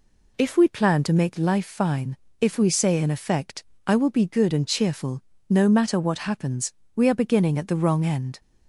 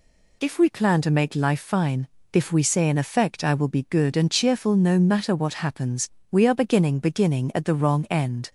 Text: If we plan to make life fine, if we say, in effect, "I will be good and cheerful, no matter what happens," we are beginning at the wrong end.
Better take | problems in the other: first | says "beginning" twice; at 6.9 s

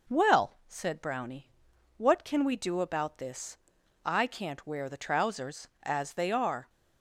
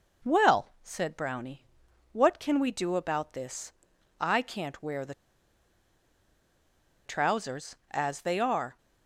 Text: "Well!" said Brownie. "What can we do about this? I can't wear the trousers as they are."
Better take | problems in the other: first | pauses between "the" and "trousers"; strong; at 5.1 s; 1.9 s long

